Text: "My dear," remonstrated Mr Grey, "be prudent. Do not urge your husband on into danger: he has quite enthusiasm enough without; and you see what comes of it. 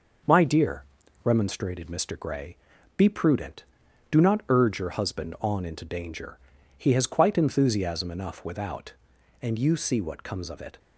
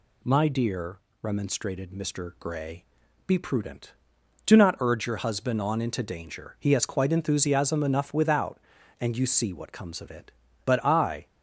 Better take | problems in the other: first | goes on to say "But I"; noticeable; from 10.6 s on; 0.62 s long

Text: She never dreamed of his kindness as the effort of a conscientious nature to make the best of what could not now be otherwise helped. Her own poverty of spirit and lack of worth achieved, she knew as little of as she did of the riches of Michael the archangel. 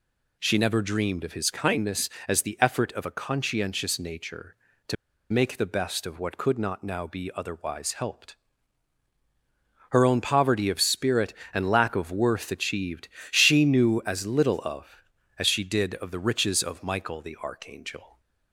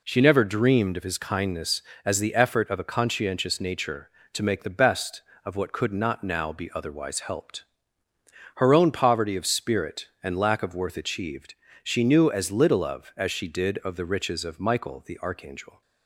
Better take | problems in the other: second | pauses between "to" and "make"; at 4.9 s; 0.36 s long

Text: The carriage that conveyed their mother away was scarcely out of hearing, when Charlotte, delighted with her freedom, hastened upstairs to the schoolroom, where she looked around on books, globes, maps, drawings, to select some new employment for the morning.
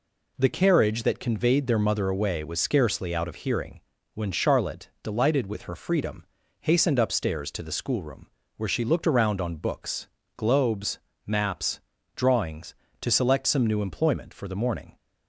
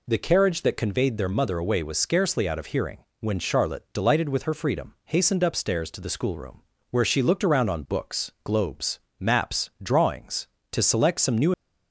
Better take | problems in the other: first | stops before "employment for the morning"; at 11.5 s

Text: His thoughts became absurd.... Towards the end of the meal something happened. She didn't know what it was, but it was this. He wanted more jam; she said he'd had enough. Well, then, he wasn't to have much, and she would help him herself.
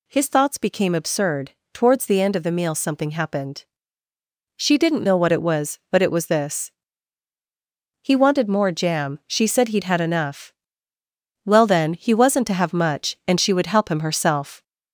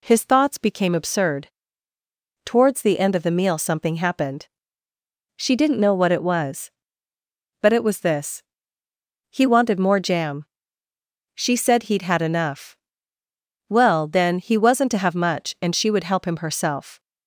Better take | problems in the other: second | gets louder; slight; throughout; 3 dB

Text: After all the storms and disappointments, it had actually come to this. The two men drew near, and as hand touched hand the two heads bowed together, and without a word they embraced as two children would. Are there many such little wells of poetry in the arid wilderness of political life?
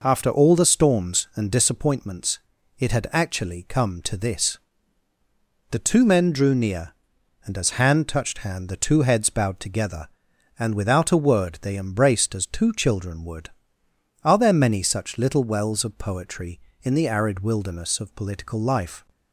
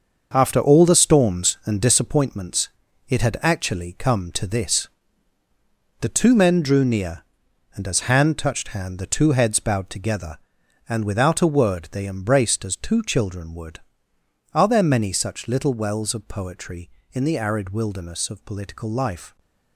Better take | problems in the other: first | gets quieter; strong; throughout; 8.5 dB

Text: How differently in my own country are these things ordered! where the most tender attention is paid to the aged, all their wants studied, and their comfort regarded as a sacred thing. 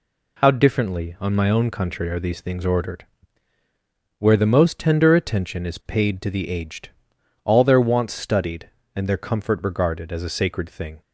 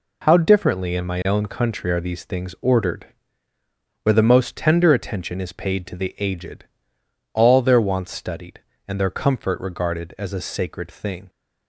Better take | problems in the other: second | says "on" for "in"; at 1.1 s

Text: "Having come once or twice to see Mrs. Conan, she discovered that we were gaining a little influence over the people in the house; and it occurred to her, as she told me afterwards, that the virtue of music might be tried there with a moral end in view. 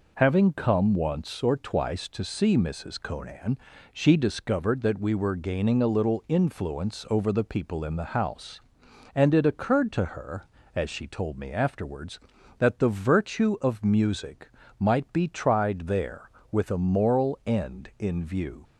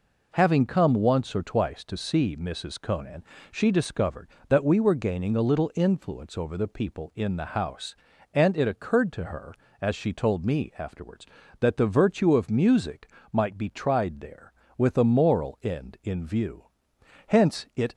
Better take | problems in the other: first | pauses between "music" and "might"; slight; at 13.0 s; 0.24 s long; slight in the first // goes on to say "Hence it"; noticeable; from 17.2 s on; 0.68 s long

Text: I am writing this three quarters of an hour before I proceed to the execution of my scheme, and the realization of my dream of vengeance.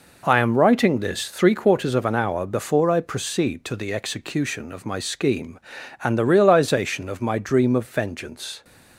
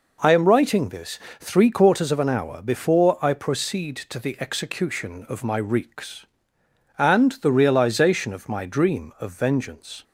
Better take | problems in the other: first | pauses between "this" and "three"; slight; at 1.1 s; 0.22 s long // says "reeks" for "scheme"; at 5.5 s

